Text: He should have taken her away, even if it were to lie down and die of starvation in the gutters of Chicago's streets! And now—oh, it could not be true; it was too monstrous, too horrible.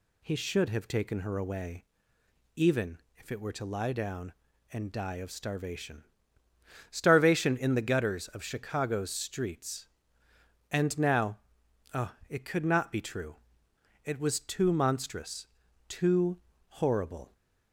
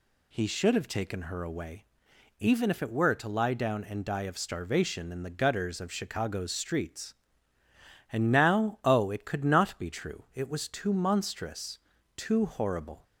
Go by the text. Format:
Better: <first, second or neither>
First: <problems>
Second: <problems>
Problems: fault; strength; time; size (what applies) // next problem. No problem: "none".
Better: second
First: pauses between "even" and "if"; slight; at 2.9 s; 0.20 s long // says "starvation" twice; at 6.8 s // pauses between "too" and "horrible"; slight; at 16.3 s; 0.30 s long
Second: none